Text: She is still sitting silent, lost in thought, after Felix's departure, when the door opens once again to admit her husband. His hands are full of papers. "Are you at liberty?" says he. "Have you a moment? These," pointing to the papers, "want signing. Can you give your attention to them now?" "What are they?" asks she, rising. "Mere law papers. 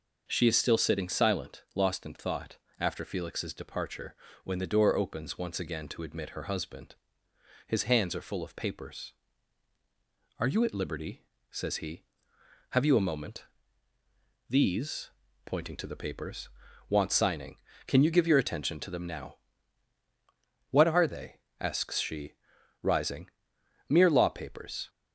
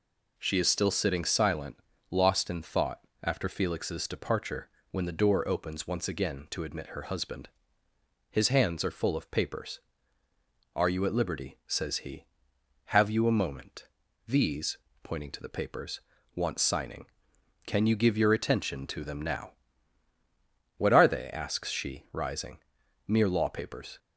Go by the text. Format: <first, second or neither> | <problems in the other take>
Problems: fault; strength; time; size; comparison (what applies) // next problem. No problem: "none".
neither | none